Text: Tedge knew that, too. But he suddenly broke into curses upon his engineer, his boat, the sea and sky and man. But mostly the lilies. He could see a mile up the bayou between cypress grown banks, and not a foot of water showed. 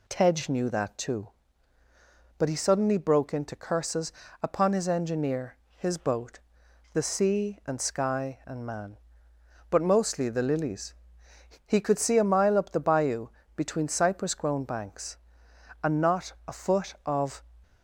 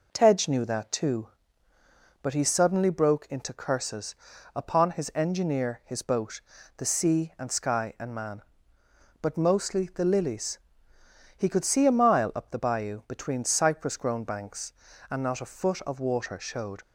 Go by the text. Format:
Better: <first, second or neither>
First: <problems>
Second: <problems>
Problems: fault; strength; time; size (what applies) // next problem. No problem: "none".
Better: second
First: pauses between "curses" and "upon"; slight; at 4.1 s; 0.30 s long // pauses between "bayou" and "between"; slight; at 13.2 s; 0.26 s long // stops before "water showed"; at 17.6 s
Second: pauses between "curses" and "upon"; at 4.1 s; 0.40 s long